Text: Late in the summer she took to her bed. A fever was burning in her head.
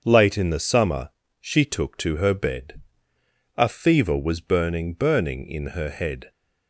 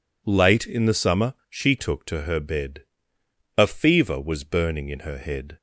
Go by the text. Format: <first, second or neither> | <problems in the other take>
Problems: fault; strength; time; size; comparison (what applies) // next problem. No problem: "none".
second | starts louder than the rest; until 1.0 s; 7 dB // pauses between "summer" and "she"; slight; at 1.1 s; 0.30 s long; slight in the second // says "burning" twice; at 4.9 s